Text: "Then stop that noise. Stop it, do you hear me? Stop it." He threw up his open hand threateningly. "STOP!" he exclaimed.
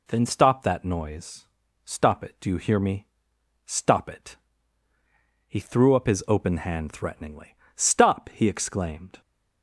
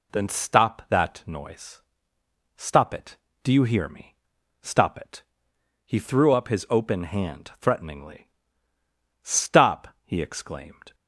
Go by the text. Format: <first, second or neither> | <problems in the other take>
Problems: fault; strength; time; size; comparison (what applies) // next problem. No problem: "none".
neither | none